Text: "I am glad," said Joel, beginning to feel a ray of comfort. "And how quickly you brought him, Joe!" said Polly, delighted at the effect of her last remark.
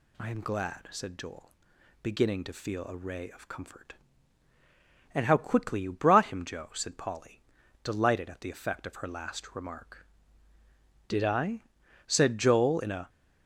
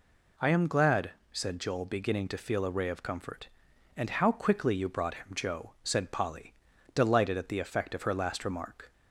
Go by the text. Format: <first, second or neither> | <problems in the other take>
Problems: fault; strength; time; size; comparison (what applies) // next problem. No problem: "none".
second | goes on to say "Did I said Joel in a"; strong; from 11.0 s on; 2.0 s long